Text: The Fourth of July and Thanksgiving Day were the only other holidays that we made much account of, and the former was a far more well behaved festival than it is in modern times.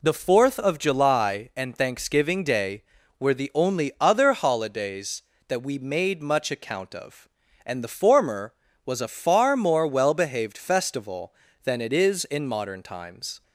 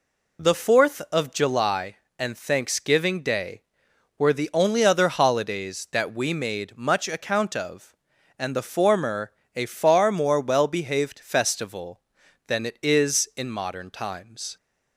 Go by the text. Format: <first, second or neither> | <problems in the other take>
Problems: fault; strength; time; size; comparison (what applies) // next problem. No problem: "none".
first | skips "was"; at 9.4 s